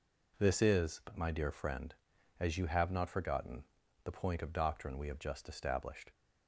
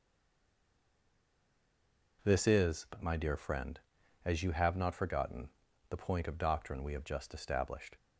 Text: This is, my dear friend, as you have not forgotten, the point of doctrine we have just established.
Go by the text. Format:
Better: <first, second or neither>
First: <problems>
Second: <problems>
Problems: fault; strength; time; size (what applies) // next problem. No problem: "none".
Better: first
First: none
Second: stays silent before the first word; until 2.1 s; 2.1 s long